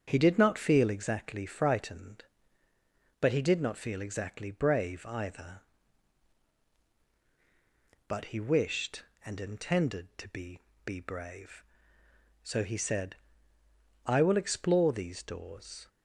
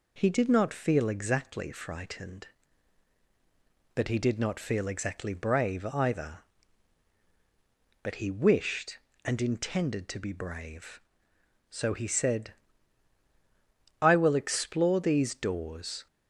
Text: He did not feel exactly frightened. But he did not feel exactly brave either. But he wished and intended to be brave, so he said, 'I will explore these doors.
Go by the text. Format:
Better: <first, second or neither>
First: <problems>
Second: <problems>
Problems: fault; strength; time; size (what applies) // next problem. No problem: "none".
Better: second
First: starts louder than the rest; strong; until 1.0 s; 7.5 dB // says "be" twice; at 10.8 s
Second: none